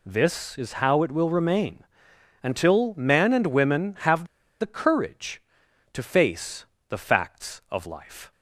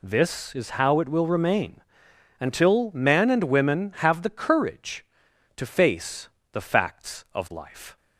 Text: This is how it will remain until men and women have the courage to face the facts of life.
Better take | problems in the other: second | pauses between "remain" and "until"; noticeable; at 1.8 s; 0.60 s long; noticeable in the second // pauses between "have" and "the"; slight; at 4.2 s; 0.35 s long // pauses between "face" and "the"; slight; at 6.6 s; 0.24 s long; slight in the second

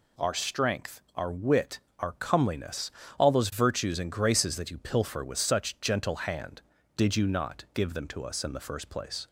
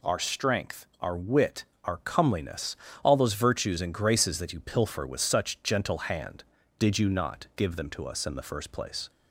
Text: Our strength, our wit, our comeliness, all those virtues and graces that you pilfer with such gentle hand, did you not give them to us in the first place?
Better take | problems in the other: neither | none

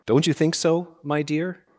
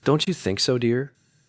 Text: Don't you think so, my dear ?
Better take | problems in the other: first | skips "my"; at 0.7 s

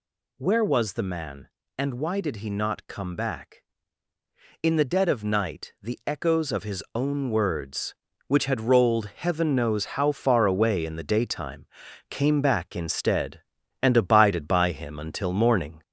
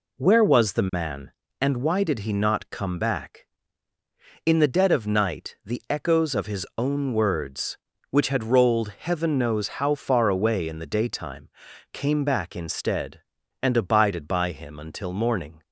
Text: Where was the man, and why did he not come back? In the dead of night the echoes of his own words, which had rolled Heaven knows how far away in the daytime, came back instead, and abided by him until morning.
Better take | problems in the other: second | gets louder; slight; throughout; 3.5 dB

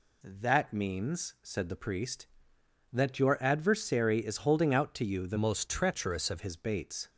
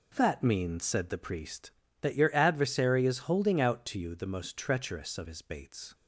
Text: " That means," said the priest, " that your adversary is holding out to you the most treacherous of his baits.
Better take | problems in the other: second | changes voice from "most" to "of"; from 5.3 to 6.4 s; 1.1 s long

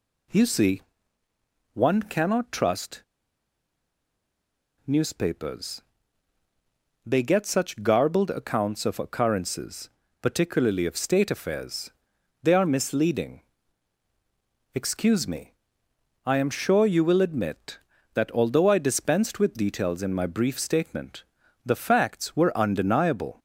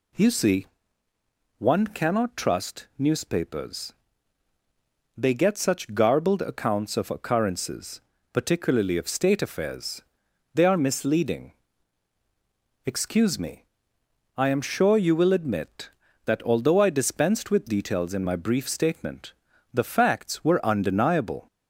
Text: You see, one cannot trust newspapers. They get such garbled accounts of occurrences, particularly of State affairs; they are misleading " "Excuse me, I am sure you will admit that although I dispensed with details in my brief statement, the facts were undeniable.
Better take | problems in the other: second | pauses between "trust" and "newspapers"; strong; at 3.0 s; 1.8 s long

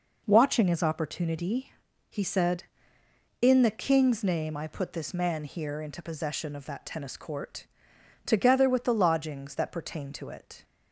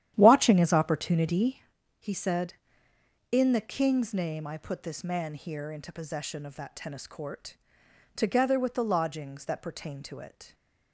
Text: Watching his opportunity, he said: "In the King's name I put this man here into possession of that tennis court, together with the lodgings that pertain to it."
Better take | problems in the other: first | starts louder than the rest; strong; until 1.6 s; 11 dB

